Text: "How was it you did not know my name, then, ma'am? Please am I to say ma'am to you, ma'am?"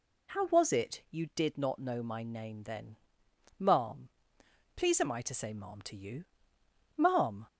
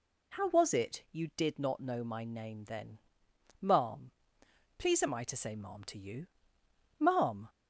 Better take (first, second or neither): neither